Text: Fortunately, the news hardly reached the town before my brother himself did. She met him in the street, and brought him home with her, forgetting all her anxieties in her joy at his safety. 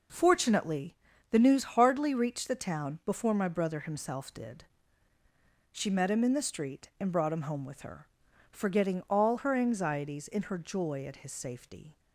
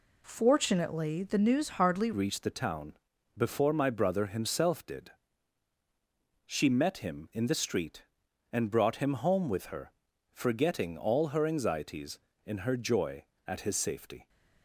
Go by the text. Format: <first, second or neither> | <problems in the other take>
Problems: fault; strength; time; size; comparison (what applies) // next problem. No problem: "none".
first | changes voice at "reached"; from 2.1 s on; 12.1 s long // pauses between "town" and "before"; at 2.9 s; 0.42 s long